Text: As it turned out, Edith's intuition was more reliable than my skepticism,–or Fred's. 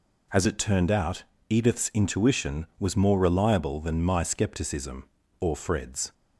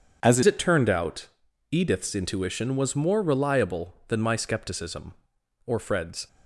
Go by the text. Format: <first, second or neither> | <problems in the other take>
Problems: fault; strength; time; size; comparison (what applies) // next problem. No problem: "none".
first | changes voice at "it"; from 0.4 s on; 5.8 s long